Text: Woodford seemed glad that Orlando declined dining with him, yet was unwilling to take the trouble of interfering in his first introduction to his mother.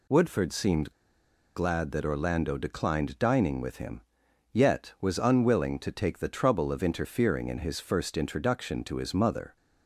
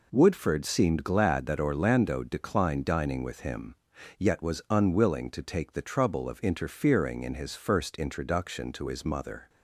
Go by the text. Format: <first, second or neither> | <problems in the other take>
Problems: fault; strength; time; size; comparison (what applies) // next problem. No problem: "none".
second | pauses between "seemed" and "glad"; noticeable; at 0.9 s; 0.63 s long